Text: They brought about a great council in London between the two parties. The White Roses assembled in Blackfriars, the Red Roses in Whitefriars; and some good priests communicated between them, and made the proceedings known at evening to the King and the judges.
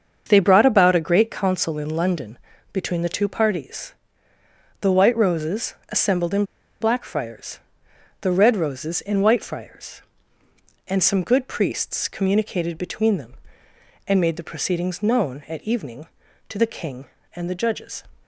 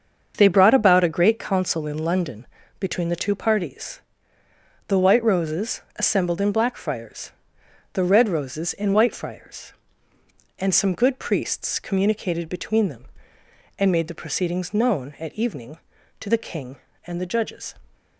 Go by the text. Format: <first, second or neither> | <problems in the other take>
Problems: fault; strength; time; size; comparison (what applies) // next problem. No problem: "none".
second | starts louder than the rest; until 1.3 s; 7 dB; also in the second // pauses between "London" and "between"; slight; at 2.3 s; 0.36 s long; slight in the second // pauses between "in" and "Blackfriars"; at 6.4 s; 0.37 s long